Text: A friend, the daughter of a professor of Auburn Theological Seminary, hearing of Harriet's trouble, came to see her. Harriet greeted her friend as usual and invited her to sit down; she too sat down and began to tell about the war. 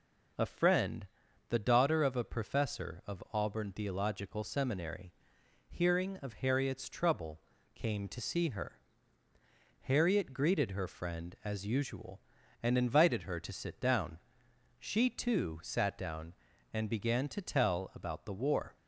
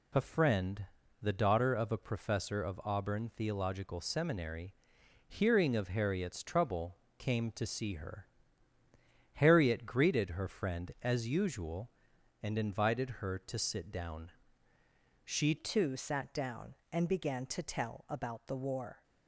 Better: first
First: none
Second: changes voice at "too"; from 15.5 s on; 3.5 s long

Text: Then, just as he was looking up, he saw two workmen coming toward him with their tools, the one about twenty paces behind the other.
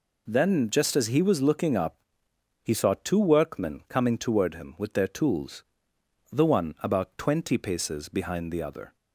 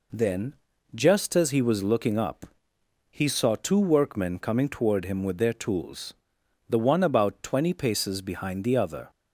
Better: neither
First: none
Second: none

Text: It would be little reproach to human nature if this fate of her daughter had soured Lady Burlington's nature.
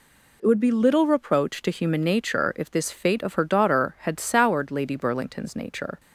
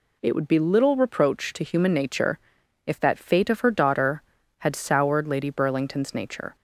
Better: first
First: none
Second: pauses between "nature" and "if"; noticeable; at 2.3 s; 0.46 s long // says "that" for "this"; at 2.9 s

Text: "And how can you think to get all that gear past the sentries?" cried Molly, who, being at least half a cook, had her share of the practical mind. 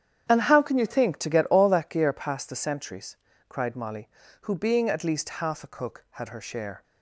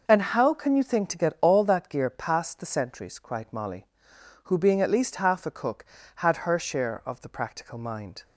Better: second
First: starts louder than the rest; strong; until 1.2 s; 9 dB // stops before "of the practical mind"; at 6.8 s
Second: none

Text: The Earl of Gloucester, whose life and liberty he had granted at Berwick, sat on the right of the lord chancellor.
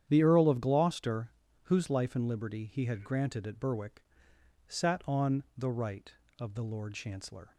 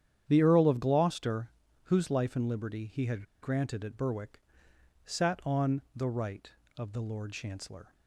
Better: first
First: starts louder than the rest; strong; until 1.0 s; 9.5 dB // pauses between "on" and "the"; slight; at 5.4 s; 0.16 s long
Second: starts louder than the rest; strong; until 1.2 s; 9.5 dB // pauses between "had" and "granted"; slight; at 3.2 s; 0.19 s long // pauses between "on" and "the"; slight; at 5.7 s; 0.16 s long

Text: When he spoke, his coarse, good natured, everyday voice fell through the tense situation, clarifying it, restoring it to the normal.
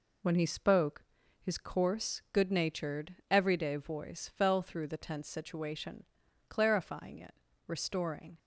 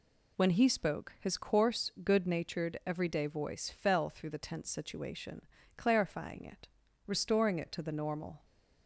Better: second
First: stops before "it to the normal"; at 8.3 s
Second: none

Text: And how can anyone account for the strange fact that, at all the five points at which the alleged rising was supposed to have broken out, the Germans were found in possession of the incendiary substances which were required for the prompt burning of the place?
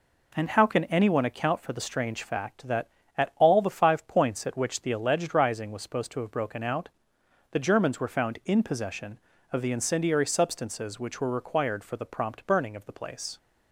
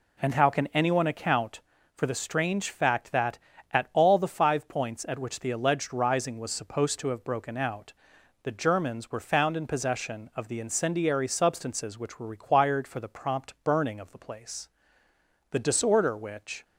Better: first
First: none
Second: goes on to say "The disorder which"; noticeable; from 15.5 s on; 1.1 s long

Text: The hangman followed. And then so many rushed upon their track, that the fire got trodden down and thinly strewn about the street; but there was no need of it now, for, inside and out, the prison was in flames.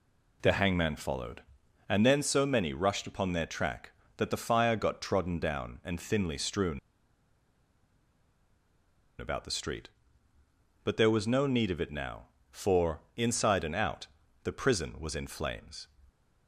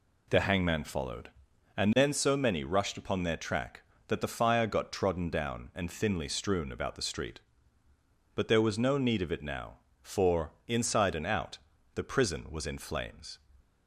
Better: second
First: pauses between "strewn" and "about"; strong; at 6.7 s; 2.3 s long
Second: none

